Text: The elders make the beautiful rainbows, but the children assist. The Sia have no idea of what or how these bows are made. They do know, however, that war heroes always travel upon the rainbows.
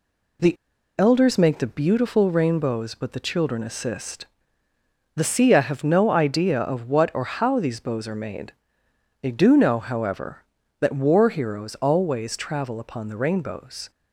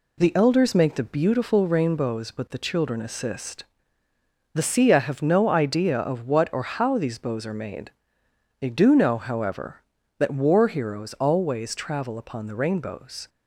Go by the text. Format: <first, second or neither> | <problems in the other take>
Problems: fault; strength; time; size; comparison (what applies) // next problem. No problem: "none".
second | pauses between "The" and "elders"; at 0.5 s; 0.42 s long